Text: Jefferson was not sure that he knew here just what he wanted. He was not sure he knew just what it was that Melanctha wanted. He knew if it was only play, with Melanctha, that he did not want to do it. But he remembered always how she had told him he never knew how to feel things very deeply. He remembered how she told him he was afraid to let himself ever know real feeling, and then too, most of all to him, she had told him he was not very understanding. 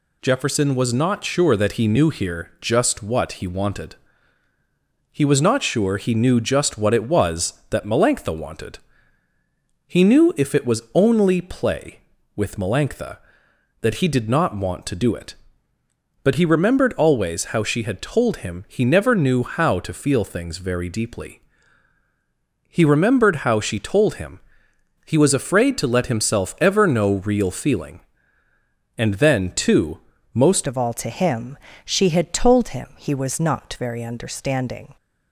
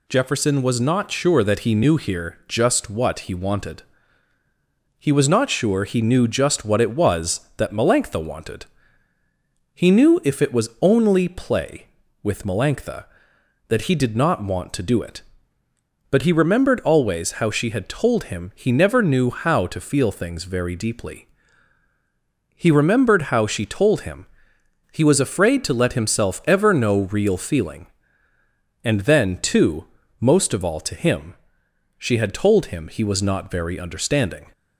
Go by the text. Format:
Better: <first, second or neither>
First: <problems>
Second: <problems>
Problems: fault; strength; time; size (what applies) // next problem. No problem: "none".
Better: second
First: pauses between "him" and "he"; noticeable; at 24.3 s; 0.66 s long // changes voice at "of"; from 30.6 s on; 4.3 s long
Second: pauses between "him" and "he"; noticeable; at 24.2 s; 0.66 s long